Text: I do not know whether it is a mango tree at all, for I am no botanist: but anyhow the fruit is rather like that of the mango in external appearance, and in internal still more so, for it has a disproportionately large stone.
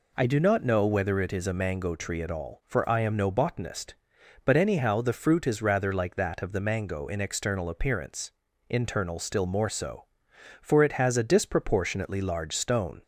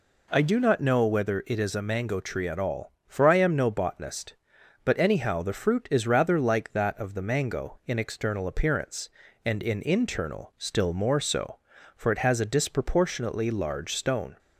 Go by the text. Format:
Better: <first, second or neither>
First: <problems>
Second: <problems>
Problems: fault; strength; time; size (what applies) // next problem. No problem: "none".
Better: second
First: skips "and in"; at 8.4 s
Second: none